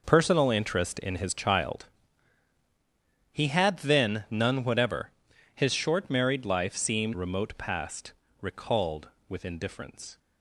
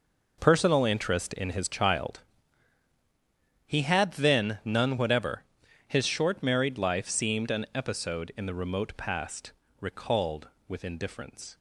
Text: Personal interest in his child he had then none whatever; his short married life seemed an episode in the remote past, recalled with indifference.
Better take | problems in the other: second | pauses between "child" and "he"; strong; at 1.8 s; 1.4 s long; strong in the second // skips "an episode in the"; at 7.1 s

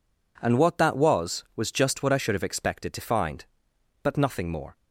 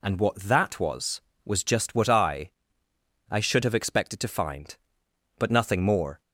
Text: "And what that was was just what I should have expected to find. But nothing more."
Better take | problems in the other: first | says "I" twice; at 3.2 s

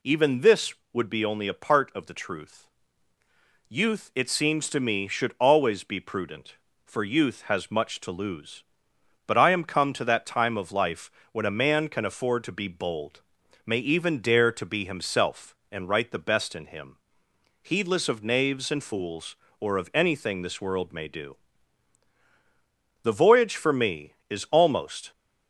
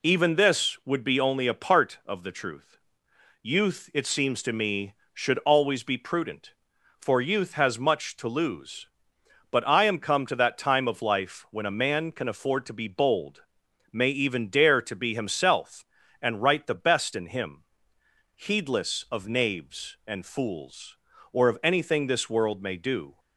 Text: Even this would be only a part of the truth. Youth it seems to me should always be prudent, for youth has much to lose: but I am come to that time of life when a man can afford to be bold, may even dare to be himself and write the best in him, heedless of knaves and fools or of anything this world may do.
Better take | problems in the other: second | pauses between "life" and "when"; slight; at 11.1 s; 0.22 s long // goes on to say "The voyage for me is almost"; strong; from 23.0 s on; 2.0 s long

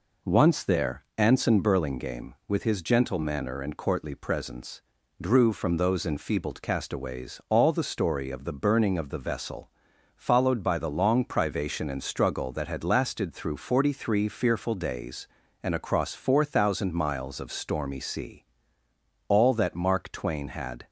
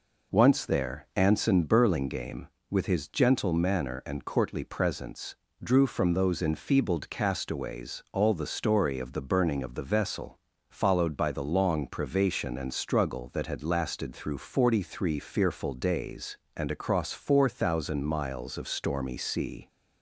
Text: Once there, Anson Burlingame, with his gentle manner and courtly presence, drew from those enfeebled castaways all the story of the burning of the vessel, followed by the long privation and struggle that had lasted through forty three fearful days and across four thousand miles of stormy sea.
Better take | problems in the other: second | goes on to say "All that Mark Twain had"; from 19.2 s on; 1.6 s long

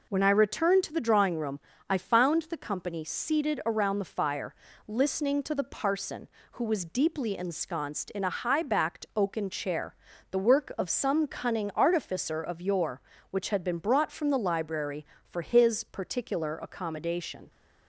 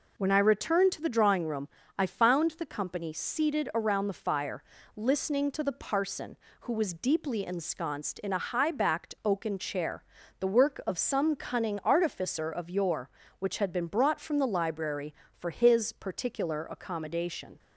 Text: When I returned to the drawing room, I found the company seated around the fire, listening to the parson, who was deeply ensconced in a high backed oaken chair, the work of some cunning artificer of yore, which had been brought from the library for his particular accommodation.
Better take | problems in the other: neither | none

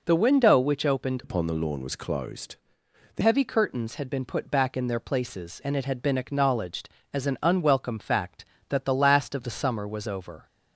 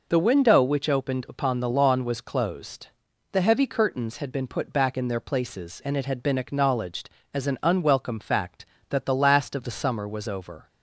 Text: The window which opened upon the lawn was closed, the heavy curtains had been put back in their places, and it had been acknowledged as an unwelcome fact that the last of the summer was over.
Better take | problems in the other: second | changes voice from "upon" to "the"; from 1.2 to 3.2 s; 2.0 s long

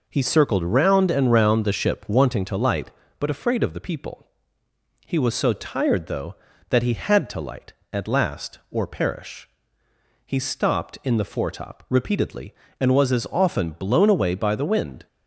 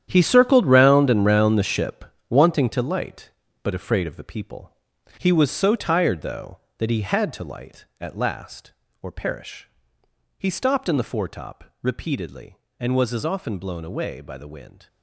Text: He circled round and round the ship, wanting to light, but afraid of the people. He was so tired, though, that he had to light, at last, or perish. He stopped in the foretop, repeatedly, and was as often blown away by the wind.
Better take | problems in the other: first | gets quieter; strong; throughout; 13 dB

